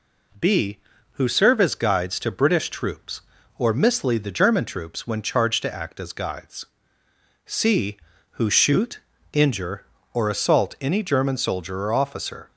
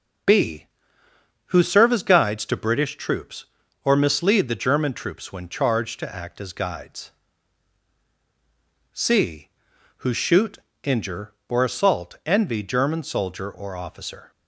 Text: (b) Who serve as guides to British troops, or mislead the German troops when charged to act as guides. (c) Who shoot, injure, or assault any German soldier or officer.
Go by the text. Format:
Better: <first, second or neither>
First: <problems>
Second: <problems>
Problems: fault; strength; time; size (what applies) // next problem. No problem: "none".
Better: first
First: none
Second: says "envy" for "any"; at 12.2 s